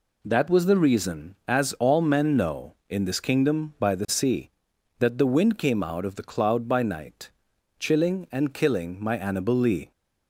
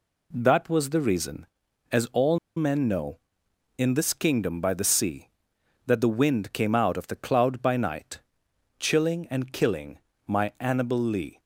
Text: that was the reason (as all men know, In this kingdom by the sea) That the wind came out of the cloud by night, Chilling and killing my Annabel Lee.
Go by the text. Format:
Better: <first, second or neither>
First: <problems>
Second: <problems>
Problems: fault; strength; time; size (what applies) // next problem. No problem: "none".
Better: first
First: none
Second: pauses between "all" and "men"; slight; at 2.3 s; 0.19 s long // pauses between "killing" and "my"; slight; at 9.9 s; 0.28 s long